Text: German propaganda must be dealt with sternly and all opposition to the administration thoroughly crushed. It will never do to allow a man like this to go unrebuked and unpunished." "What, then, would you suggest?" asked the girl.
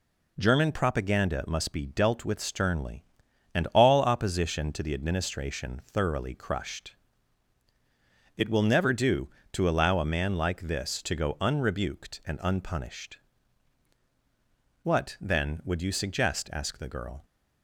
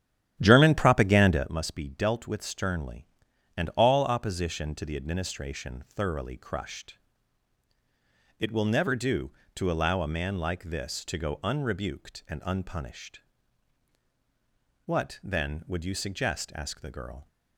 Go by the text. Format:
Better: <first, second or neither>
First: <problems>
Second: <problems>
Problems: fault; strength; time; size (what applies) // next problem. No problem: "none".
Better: first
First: none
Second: starts louder than the rest; strong; until 1.5 s; 10.5 dB